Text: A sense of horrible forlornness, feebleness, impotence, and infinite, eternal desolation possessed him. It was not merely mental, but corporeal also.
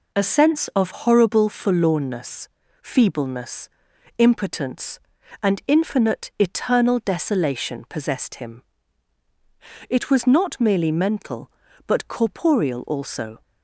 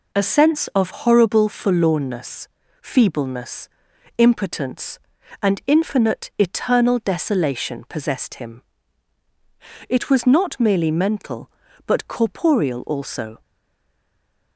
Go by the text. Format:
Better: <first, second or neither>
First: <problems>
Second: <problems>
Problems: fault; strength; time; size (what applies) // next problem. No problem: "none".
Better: first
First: none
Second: stays silent after the last word; noticeable; from 13.4 s on; 1.1 s long